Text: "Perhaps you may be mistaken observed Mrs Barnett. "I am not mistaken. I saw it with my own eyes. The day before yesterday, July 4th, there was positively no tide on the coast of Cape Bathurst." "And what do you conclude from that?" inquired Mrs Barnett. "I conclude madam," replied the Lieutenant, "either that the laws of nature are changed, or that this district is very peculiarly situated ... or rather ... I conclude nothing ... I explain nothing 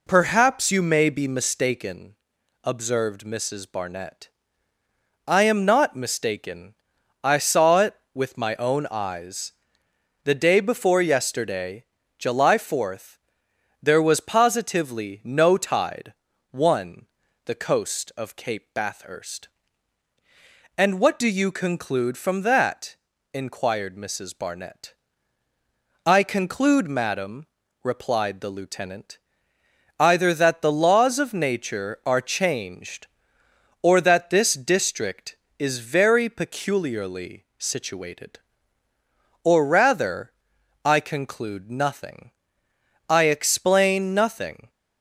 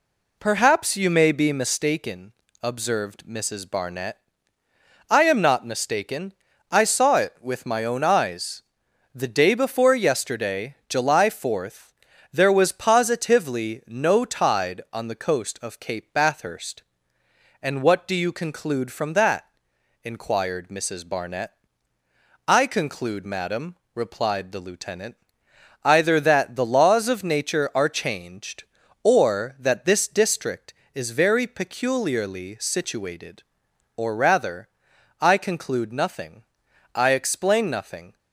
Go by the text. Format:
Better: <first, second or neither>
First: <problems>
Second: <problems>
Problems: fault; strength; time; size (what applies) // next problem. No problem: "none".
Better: second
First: pauses between "mistaken" and "observed"; noticeable; at 2.1 s; 0.48 s long // says "one" for "on"; at 16.5 s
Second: pauses between "mistaken" and "observed"; slight; at 2.3 s; 0.30 s long